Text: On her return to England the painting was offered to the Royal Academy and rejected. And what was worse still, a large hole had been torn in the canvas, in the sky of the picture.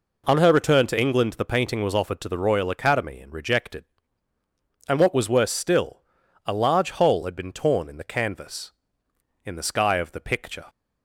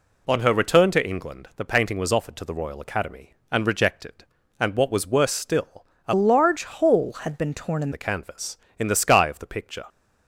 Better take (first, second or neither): first